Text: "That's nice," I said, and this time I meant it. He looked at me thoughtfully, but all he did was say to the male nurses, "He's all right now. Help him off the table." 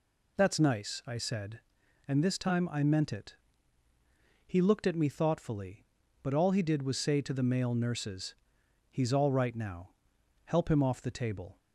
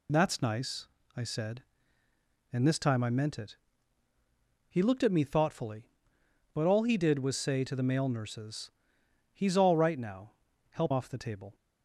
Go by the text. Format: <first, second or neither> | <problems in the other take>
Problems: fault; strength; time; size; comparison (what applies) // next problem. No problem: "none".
first | skips "him"; at 10.9 s